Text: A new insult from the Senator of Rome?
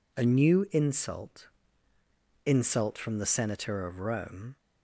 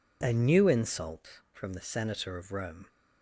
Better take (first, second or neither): second